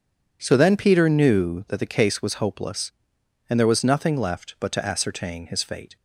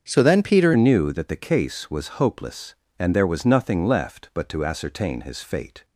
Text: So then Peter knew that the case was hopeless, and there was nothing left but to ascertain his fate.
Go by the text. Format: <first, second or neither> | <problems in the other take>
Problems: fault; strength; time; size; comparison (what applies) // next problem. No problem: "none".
first | starts louder than the rest; until 1.0 s; 7 dB // changes voice at "knew"; from 0.7 s on; 5.1 s long